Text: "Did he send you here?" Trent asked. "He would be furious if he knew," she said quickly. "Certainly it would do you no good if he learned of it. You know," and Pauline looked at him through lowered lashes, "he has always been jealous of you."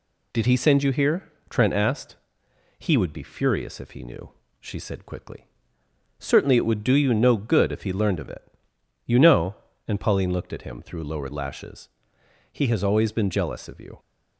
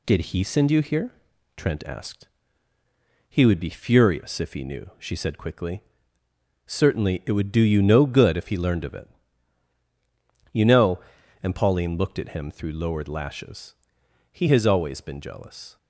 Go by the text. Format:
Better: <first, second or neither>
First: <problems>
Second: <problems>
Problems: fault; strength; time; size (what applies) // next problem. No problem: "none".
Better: first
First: none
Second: stops before "of you"; at 15.7 s